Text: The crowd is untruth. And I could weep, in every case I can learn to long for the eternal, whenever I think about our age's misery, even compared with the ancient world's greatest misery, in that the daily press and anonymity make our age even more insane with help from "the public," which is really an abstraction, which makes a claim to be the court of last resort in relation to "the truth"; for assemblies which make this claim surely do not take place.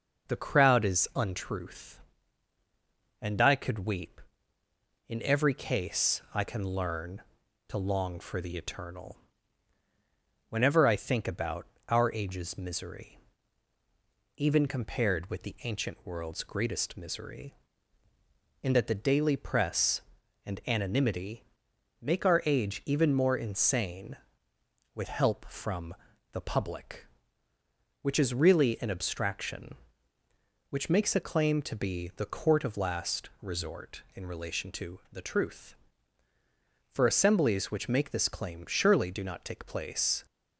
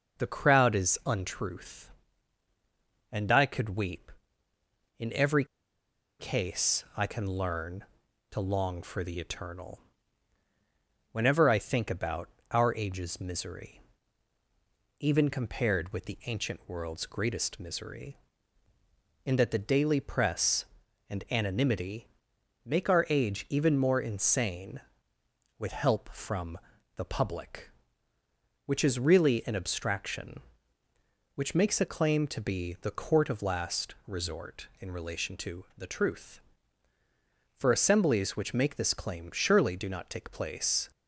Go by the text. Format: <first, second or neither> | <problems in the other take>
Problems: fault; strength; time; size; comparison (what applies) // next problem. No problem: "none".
first | pauses between "every" and "case"; noticeable; at 5.4 s; 0.75 s long // pauses between "about" and "our"; slight; at 12.2 s; 0.22 s long; slight in the first // pauses between "anonymity" and "make"; noticeable; at 22.0 s; 0.58 s long; noticeable in the first // pauses between "from" and "the"; at 26.5 s; 0.38 s long; also in the first